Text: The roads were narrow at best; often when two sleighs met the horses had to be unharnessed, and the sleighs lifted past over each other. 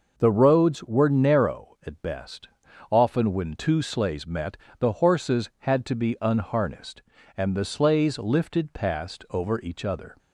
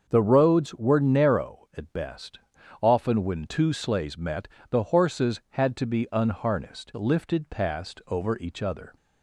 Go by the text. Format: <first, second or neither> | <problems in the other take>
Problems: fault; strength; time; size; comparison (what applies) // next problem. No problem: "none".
first | starts louder than the rest; until 1.1 s; 6.5 dB // pauses between "met" and "the"; slight; at 4.4 s; 0.22 s long; slight in the first // skips "and the sleighs"; at 6.9 s